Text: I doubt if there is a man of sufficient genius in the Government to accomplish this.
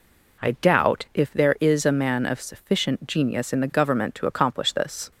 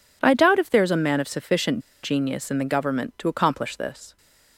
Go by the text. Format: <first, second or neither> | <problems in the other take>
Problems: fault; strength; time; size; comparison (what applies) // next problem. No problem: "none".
first | pauses between "sufficient" and "genius"; slight; at 1.8 s; 0.22 s long